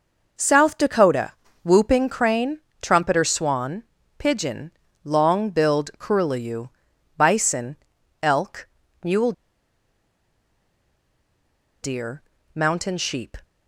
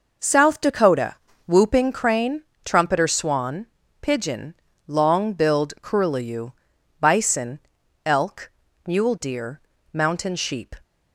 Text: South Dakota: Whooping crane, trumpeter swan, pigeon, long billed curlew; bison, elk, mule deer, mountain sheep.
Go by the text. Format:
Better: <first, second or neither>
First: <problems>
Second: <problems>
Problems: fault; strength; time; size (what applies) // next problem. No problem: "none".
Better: second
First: pauses between "mule" and "deer"; strong; at 9.3 s; 2.5 s long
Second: none